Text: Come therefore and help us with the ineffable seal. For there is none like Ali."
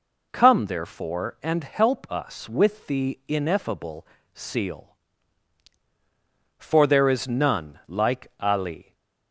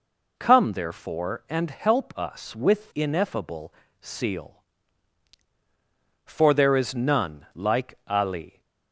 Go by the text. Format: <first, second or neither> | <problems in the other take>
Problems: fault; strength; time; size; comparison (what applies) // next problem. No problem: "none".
first | skips "the"; at 2.9 s // pauses between "ineffable" and "seal"; slight; at 3.7 s; 0.28 s long; slight in the first